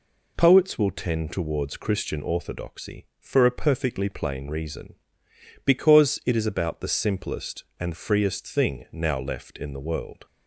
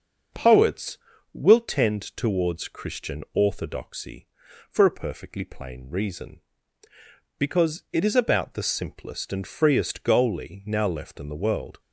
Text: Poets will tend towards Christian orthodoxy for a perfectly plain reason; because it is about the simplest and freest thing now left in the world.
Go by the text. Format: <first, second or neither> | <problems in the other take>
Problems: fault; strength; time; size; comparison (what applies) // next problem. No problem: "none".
first | starts louder than the rest; until 1.7 s; 6.5 dB // says "goalie" for "thing"; at 10.0 s